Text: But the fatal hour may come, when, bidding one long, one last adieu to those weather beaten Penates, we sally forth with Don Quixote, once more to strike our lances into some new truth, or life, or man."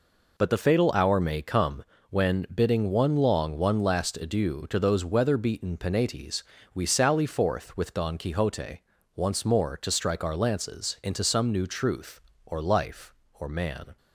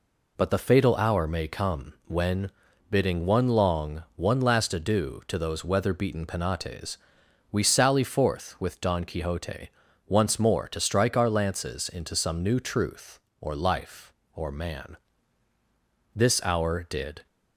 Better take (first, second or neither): first